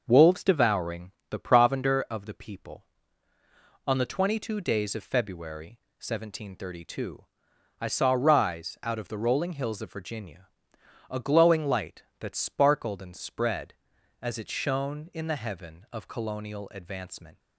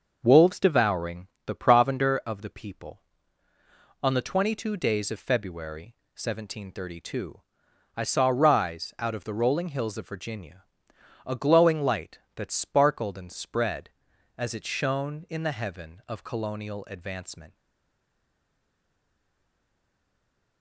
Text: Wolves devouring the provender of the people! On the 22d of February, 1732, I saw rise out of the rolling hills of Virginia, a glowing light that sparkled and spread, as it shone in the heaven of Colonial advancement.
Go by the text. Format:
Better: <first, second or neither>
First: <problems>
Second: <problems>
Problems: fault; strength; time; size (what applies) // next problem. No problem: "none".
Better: first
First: starts louder than the rest; until 1.0 s; 6.5 dB // pauses between "devouring" and "the"; slight; at 1.1 s; 0.20 s long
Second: starts louder than the rest; until 1.2 s; 6.5 dB // pauses between "devouring" and "the"; slight; at 1.2 s; 0.20 s long // stays silent after the last word; strong; from 17.5 s on; 3.1 s long